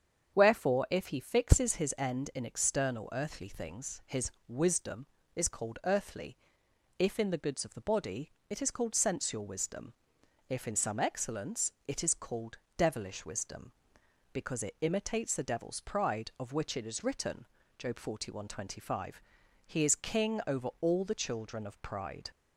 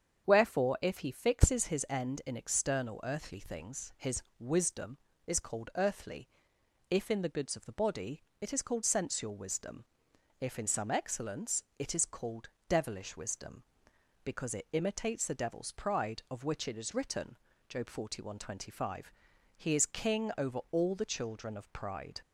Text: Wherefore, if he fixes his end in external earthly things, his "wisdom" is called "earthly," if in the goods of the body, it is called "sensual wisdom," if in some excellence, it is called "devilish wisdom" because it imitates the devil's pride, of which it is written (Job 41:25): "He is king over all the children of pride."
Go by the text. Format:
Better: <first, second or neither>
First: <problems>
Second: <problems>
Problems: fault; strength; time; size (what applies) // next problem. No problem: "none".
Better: neither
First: starts louder than the rest; strong; until 1.3 s; 7.5 dB // pauses between "his" and "wisdom"; slight; at 4.3 s; 0.16 s long // pauses between "called" and "devilish"; slight; at 12.5 s; 0.22 s long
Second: starts louder than the rest; strong; until 1.3 s; 7.5 dB // pauses between "his" and "wisdom"; slight; at 4.2 s; 0.16 s long // pauses between "called" and "devilish"; slight; at 12.4 s; 0.22 s long